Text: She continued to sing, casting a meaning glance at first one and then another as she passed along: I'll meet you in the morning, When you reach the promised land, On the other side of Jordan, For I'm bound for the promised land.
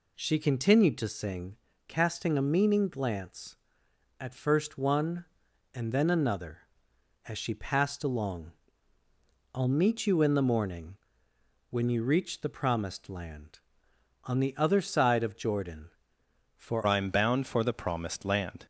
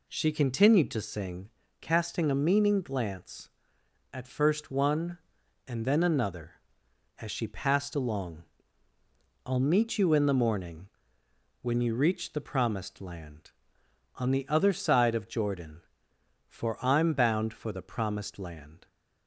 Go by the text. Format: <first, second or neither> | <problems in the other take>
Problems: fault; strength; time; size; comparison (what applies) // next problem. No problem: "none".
second | changes voice at "I'm"; from 16.8 s on; 1.8 s long